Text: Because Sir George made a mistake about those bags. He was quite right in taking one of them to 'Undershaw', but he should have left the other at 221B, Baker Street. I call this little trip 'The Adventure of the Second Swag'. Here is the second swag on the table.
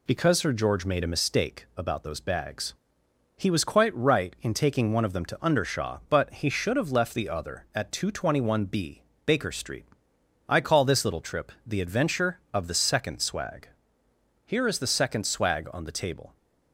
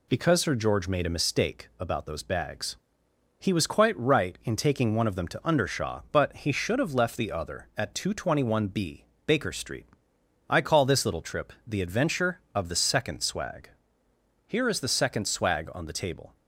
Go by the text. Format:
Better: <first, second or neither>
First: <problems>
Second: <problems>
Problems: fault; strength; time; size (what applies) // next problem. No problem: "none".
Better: neither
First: pauses between "trip" and "The"; slight; at 11.5 s; 0.16 s long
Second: pauses between "trip" and "The"; slight; at 11.5 s; 0.16 s long